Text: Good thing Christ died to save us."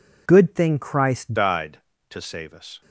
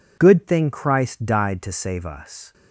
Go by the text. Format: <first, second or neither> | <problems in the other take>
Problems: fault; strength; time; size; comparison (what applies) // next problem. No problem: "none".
second | changes voice at "died"; from 1.3 s on; 1.5 s long